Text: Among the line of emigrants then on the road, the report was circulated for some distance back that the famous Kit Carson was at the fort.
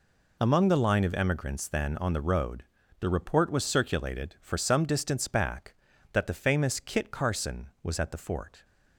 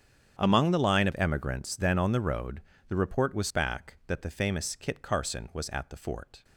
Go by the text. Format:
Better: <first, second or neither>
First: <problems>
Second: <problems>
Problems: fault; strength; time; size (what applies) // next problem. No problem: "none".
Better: first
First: none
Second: starts louder than the rest; strong; until 1.4 s; 8.5 dB // skips "circulated for some distance"; at 3.4 s